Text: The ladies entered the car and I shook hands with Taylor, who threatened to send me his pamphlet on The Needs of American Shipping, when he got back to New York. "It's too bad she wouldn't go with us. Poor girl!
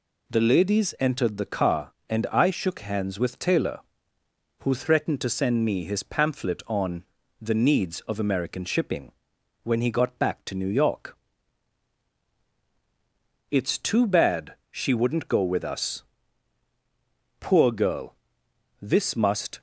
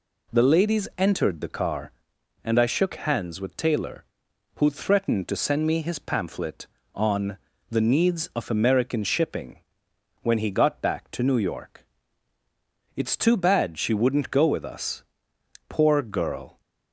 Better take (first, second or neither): second